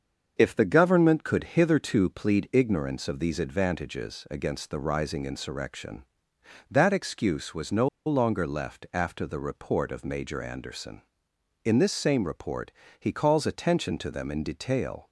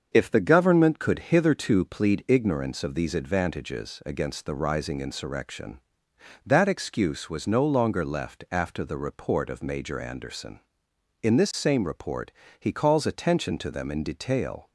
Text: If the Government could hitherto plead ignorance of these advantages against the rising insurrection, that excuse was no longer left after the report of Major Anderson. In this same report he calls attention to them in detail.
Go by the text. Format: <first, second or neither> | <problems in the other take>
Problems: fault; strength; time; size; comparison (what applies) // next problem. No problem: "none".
second | starts louder than the rest; until 1.3 s; 7 dB; also in the second // pauses between "no" and "longer"; slight; at 7.8 s; 0.19 s long // pauses between "report" and "he"; slight; at 12.6 s; 0.30 s long; slight in the second